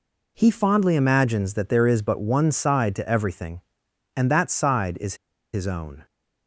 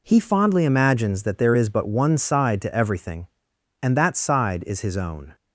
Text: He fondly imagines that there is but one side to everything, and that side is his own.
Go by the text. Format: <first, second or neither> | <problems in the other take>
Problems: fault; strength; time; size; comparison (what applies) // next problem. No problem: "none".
second | pauses between "is" and "his"; at 5.1 s; 0.38 s long